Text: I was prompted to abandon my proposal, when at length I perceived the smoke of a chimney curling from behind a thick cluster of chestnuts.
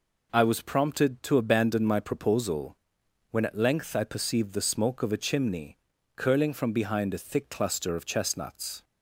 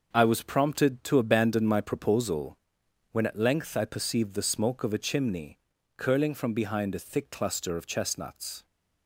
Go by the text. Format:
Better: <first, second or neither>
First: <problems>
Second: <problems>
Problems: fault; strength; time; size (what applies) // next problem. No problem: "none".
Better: first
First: pauses between "chimney" and "curling"; at 5.7 s; 0.40 s long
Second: gets quieter; strong; throughout; 7 dB // pauses between "chimney" and "curling"; at 5.5 s; 0.40 s long